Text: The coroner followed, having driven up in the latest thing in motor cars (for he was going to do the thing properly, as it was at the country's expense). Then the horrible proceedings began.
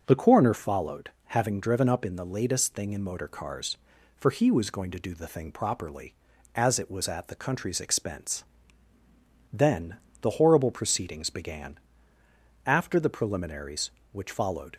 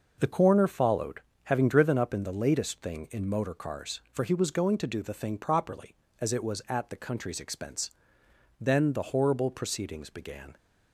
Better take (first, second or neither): second